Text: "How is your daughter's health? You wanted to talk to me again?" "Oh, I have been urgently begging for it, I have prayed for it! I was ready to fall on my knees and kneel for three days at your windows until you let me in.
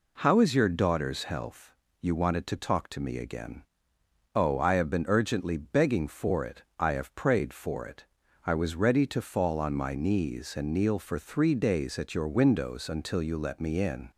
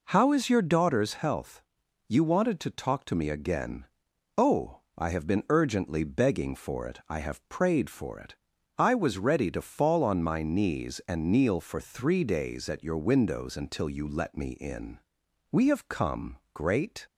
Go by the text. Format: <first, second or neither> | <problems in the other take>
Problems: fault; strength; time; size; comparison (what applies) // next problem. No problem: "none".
first | goes on to say "We have come great"; from 15.5 s on; 1.5 s long